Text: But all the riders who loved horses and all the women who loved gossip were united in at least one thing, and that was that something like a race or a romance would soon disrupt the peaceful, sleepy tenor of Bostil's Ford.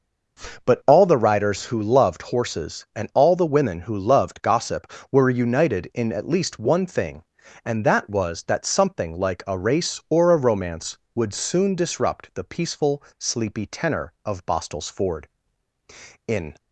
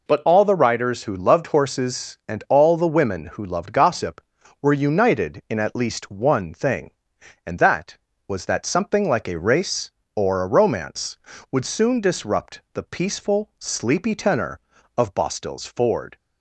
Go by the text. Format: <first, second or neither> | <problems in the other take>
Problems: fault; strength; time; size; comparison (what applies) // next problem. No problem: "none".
second | goes on to say "In"; slight; from 16.2 s on; 0.26 s long